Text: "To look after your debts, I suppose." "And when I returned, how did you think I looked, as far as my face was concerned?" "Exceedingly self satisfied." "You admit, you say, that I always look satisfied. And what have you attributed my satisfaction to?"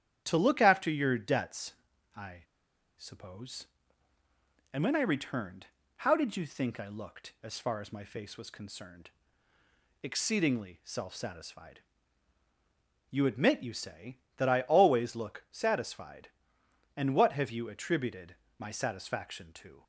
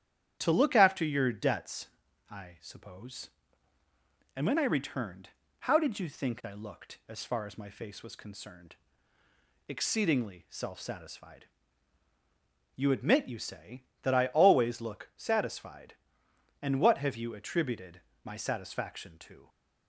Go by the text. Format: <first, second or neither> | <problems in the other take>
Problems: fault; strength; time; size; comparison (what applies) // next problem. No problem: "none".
second | starts louder than the rest; strong; until 1.2 s; 10 dB; strong in the second // pauses between "I" and "suppose"; noticeable; at 2.4 s; 0.54 s long // pauses between "attributed" and "my"; slight; at 18.3 s; 0.20 s long; slight in the second